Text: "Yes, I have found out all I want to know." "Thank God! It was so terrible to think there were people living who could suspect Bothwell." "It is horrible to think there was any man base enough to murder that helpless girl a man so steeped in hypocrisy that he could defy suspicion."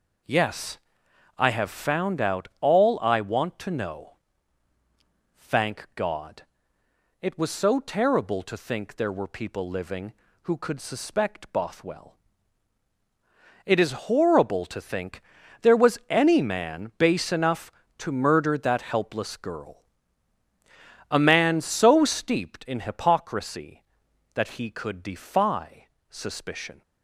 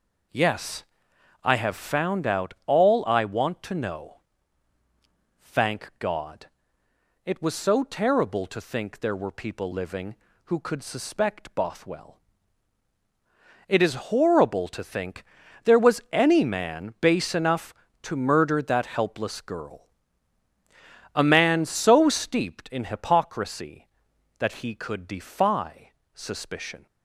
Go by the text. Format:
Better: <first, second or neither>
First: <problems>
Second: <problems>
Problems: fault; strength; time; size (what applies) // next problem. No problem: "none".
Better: neither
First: pauses between "think" and "there"; at 15.2 s; 0.40 s long // pauses between "girl" and "a"; strong; at 19.8 s; 1.2 s long // pauses between "defy" and "suspicion"; slight; at 25.8 s; 0.22 s long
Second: pauses between "think" and "there"; at 15.2 s; 0.40 s long // pauses between "girl" and "a"; strong; at 19.8 s; 1.2 s long // pauses between "defy" and "suspicion"; slight; at 25.9 s; 0.22 s long